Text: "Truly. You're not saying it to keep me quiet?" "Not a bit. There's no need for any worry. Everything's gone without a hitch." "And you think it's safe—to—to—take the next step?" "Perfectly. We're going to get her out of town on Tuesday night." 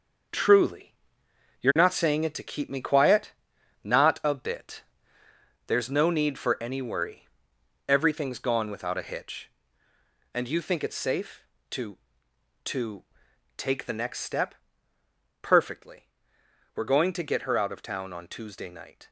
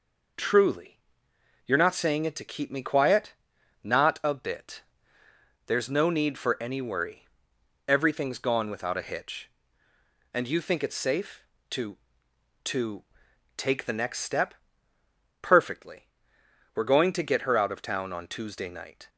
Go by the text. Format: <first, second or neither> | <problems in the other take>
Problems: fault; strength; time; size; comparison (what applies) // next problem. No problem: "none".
second | gets quieter; strong; throughout; 7 dB